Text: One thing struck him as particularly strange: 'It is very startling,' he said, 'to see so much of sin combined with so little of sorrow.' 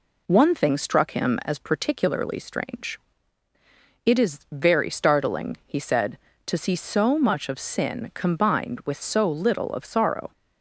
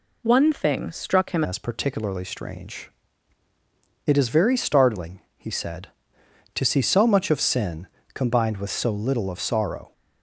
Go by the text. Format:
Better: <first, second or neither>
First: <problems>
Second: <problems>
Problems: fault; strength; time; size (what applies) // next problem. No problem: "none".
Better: first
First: none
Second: changes voice at "as"; from 1.4 s on; 8.5 s long // pauses between "sin" and "combined"; slight; at 7.8 s; 0.28 s long